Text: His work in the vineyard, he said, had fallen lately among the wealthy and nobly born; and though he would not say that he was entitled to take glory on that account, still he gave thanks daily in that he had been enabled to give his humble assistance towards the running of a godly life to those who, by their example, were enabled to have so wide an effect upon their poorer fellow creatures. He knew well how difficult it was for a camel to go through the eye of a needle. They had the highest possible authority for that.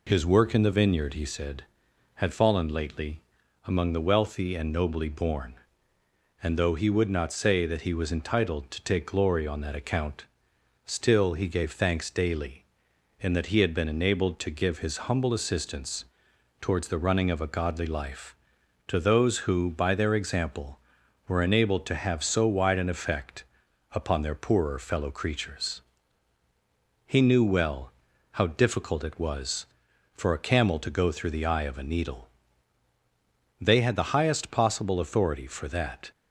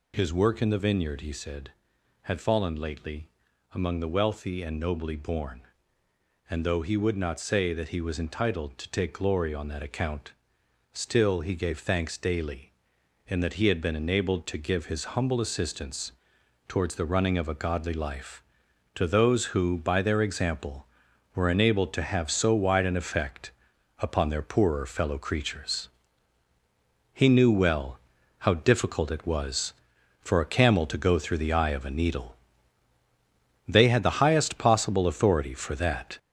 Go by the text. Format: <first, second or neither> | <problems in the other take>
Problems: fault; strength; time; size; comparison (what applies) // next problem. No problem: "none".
first | gets louder; noticeable; throughout; 6 dB // pauses between "lately" and "among"; noticeable; at 3.2 s; 0.46 s long; noticeable in the first // pauses between "assistance" and "towards"; noticeable; at 16.1 s; 0.56 s long; noticeable in the first // pauses between "effect" and "upon"; noticeable; at 23.5 s; 0.48 s long; noticeable in the first // pauses between "well" and "how"; at 27.9 s; 0.40 s long; also in the first